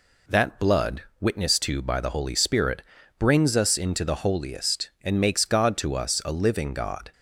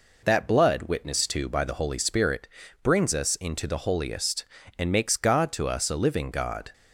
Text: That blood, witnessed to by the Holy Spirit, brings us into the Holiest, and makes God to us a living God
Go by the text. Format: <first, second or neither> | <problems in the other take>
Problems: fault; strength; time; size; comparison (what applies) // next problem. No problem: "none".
neither | none